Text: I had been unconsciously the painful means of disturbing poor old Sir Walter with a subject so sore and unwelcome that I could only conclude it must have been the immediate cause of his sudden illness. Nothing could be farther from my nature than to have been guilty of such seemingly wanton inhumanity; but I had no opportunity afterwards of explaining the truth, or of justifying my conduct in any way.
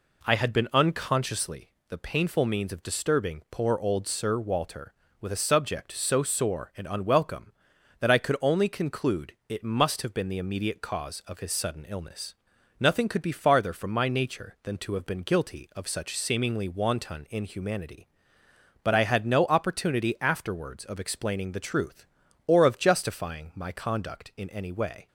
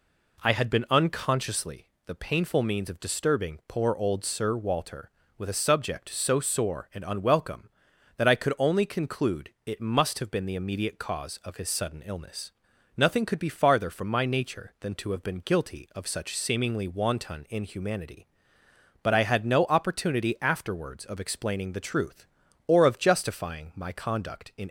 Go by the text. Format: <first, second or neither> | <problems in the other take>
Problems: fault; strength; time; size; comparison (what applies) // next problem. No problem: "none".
first | pauses between "unconsciously" and "the"; slight; at 1.8 s; 0.16 s long; slight in the first // pauses between "conclude" and "it"; slight; at 9.4 s; 0.16 s long; slight in the first // stops before "any way"; at 24.6 s